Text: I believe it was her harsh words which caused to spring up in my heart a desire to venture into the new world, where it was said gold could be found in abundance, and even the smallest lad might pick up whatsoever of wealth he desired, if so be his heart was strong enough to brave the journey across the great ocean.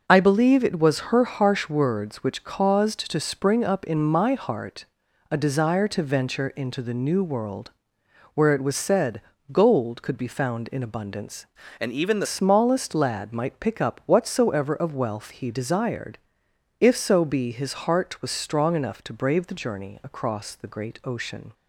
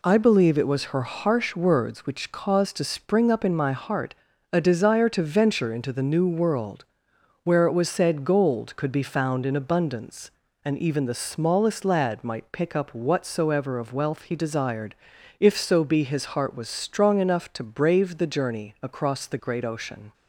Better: second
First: pauses between "heart" and "a"; noticeable; at 4.8 s; 0.46 s long // pauses between "said" and "gold"; slight; at 9.2 s; 0.32 s long // changes voice from "and" to "the"; from 11.7 to 12.2 s; 0.5 s long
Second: pauses between "heart" and "a"; slight; at 4.1 s; 0.36 s long

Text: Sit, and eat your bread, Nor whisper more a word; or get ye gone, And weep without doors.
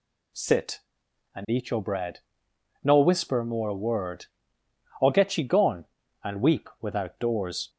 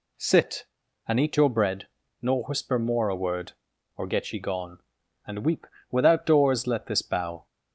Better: first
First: none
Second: pauses between "weep" and "without"; slight; at 5.6 s; 0.24 s long // goes on to say "Let this bow"; noticeable; from 6.6 s on; 0.78 s long

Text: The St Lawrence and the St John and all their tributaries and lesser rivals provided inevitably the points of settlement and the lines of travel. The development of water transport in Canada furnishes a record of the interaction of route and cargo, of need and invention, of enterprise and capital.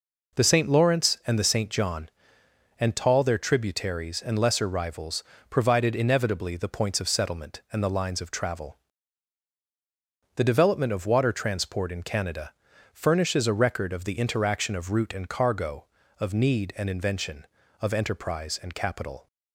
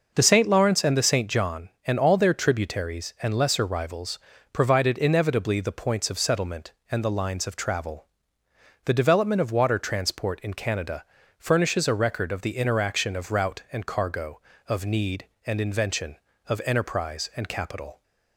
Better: second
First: says "tall" for "all"; at 2.9 s // pauses between "rivals" and "provided"; slight; at 5.2 s; 0.28 s long // pauses between "Canada" and "furnishes"; at 12.5 s; 0.44 s long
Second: pauses between "rivals" and "provided"; slight; at 4.1 s; 0.34 s long // pauses between "Canada" and "furnishes"; slight; at 11.0 s; 0.36 s long

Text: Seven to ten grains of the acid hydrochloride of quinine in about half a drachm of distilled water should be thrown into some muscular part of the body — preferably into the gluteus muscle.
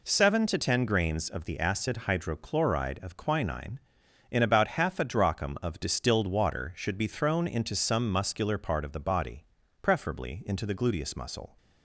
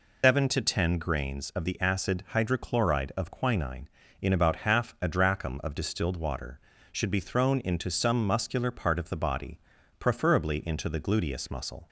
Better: first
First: none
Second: loses the start of "Seven"; at 0.2 s; 165 ms

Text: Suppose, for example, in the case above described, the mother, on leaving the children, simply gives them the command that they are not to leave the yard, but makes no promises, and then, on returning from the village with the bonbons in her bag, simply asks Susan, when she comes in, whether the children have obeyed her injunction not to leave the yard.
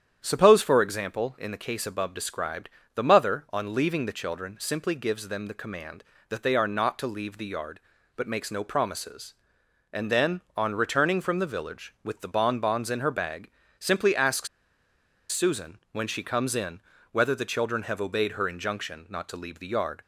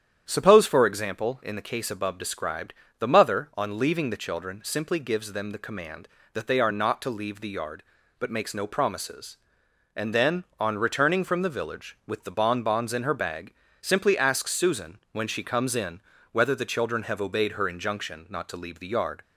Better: second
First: starts louder than the rest; strong; until 1.2 s; 9.5 dB // pauses between "asks" and "Susan"; noticeable; at 14.4 s; 0.83 s long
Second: starts louder than the rest; strong; until 1.3 s; 9.5 dB

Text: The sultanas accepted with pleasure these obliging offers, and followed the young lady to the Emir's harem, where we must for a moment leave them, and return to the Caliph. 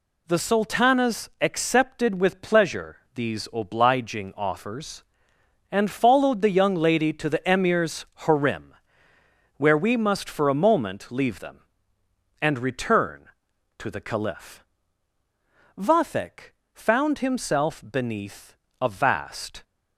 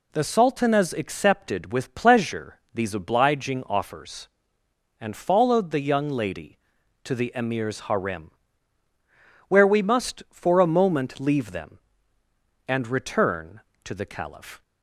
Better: second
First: pauses between "pleasure" and "these"; slight; at 2.9 s; 0.16 s long // pauses between "Emir's" and "harem"; slight; at 8.0 s; 0.20 s long // goes on to say "Vathek found himself beneath a vast"; strong; from 15.7 s on; 3.8 s long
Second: none

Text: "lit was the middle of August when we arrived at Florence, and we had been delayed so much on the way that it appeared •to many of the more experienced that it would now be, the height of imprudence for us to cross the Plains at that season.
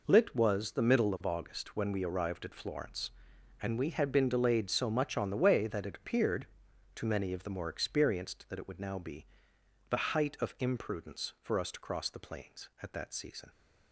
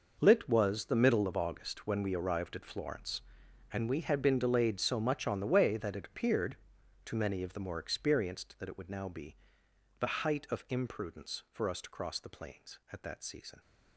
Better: first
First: none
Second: gets quieter; strong; throughout; 13 dB

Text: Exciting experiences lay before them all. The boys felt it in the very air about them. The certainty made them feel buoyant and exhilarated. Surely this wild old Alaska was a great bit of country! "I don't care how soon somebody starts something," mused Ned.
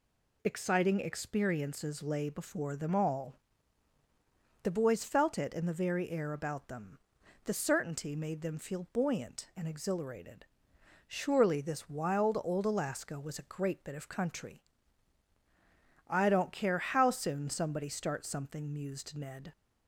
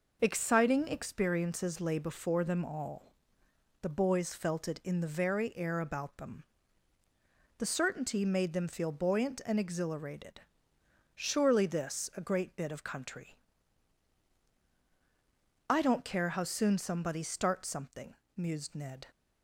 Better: first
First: none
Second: skips "wild old Alaska was"; at 12.1 s

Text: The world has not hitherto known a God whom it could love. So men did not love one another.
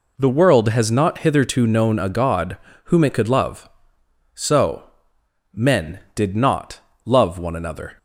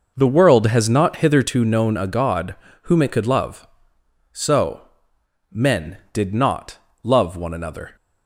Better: first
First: pauses between "God" and "whom"; slight; at 2.5 s; 0.28 s long // pauses between "So" and "men"; noticeable; at 4.8 s; 0.68 s long // pauses between "not" and "love"; slight; at 6.7 s; 0.24 s long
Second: starts louder than the rest; noticeable; until 1.6 s; 6 dB // pauses between "God" and "whom"; slight; at 2.5 s; 0.28 s long // pauses between "So" and "men"; noticeable; at 4.8 s; 0.68 s long // pauses between "not" and "love"; slight; at 6.7 s; 0.24 s long

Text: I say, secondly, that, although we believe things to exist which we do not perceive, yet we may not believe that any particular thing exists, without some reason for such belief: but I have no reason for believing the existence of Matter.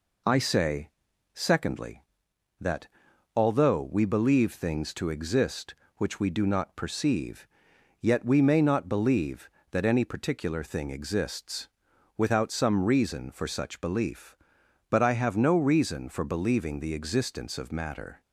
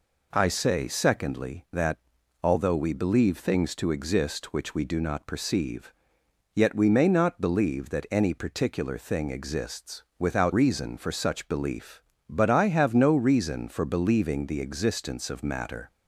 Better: first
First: none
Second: skips "some"; at 10.5 s

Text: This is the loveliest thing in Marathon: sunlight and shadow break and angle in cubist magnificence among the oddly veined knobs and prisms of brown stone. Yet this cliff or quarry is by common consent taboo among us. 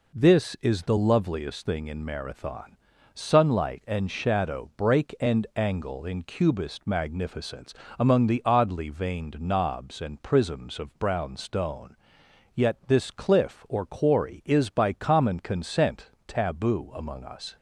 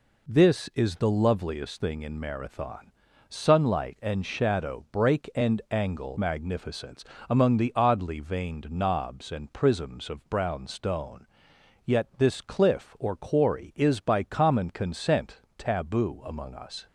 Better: first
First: pauses between "magnificence" and "among"; slight; at 7.7 s; 0.26 s long // pauses between "consent" and "taboo"; slight; at 16.0 s; 0.18 s long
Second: skips "in cubist"; at 6.1 s // pauses between "magnificence" and "among"; slight; at 7.0 s; 0.26 s long // pauses between "consent" and "taboo"; slight; at 15.4 s; 0.18 s long

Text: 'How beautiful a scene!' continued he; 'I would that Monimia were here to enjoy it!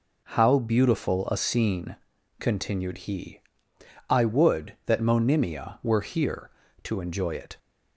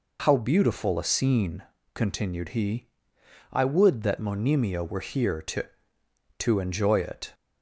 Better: first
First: none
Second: says "to" twice; at 6.3 s

